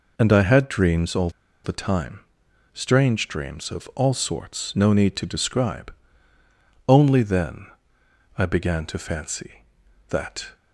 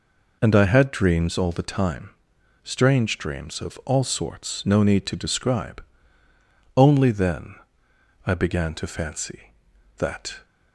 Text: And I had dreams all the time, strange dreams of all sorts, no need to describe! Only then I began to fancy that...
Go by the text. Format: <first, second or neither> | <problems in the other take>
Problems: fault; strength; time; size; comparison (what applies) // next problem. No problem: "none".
second | pauses between "all" and "the"; slight; at 1.2 s; 0.34 s long // pauses between "then" and "I"; noticeable; at 7.6 s; 0.72 s long; noticeable in the second